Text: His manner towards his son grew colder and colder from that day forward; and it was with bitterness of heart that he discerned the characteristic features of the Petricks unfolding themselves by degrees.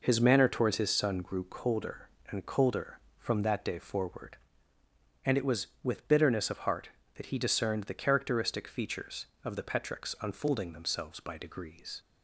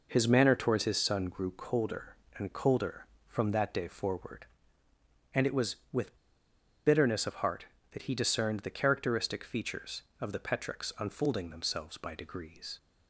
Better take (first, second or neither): first